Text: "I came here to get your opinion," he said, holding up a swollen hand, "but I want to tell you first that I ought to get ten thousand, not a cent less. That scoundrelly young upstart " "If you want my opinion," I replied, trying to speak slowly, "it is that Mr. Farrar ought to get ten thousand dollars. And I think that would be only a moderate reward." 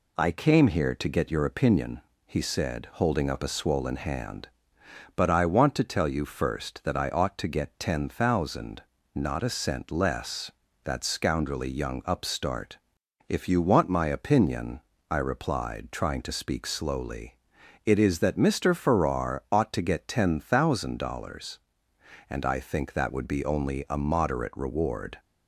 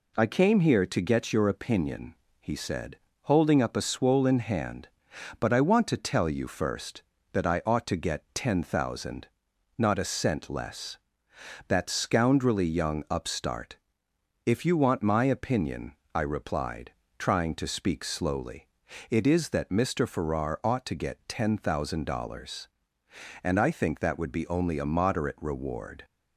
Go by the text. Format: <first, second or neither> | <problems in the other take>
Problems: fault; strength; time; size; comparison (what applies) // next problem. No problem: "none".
neither | none